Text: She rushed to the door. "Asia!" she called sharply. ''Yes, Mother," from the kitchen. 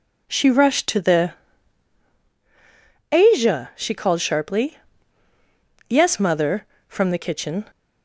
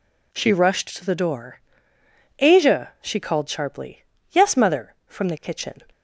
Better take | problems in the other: second | skips "door"; at 2.2 s

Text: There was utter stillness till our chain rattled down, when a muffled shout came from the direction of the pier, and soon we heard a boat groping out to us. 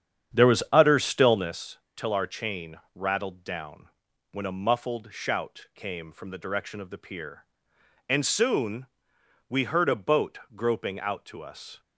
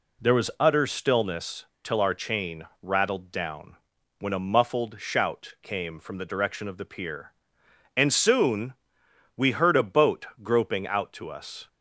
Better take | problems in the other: second | starts louder than the rest; strong; until 1.6 s; 8.5 dB // pauses between "stillness" and "till"; slight; at 1.7 s; 0.18 s long; slight in the second // pauses between "chain" and "rattled"; slight; at 2.7 s; 0.16 s long; slight in the second // pauses between "soon" and "we"; noticeable; at 8.8 s; 0.64 s long; noticeable in the second // pauses between "boat" and "groping"; slight; at 10.3 s; 0.18 s long; slight in the second

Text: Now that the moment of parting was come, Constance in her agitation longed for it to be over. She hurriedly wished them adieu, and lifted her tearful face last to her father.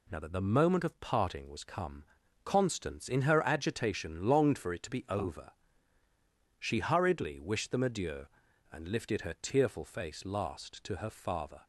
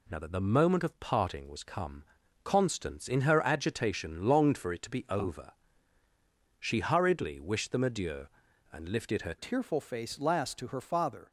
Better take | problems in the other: first | changes voice at "tearful"; from 9.3 s on; 1.9 s long

